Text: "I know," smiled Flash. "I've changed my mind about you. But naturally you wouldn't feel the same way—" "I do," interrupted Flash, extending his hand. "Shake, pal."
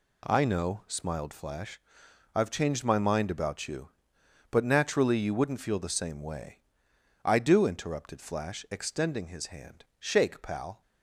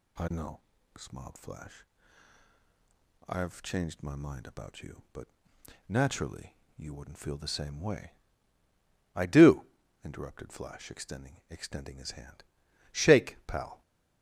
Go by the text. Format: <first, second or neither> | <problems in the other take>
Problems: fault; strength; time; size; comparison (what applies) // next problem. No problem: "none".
first | pauses between "But" and "naturally"; noticeable; at 5.2 s; 0.60 s long // pauses between "naturally" and "you"; slight; at 6.5 s; 0.22 s long // says "extending" twice; at 11.4 s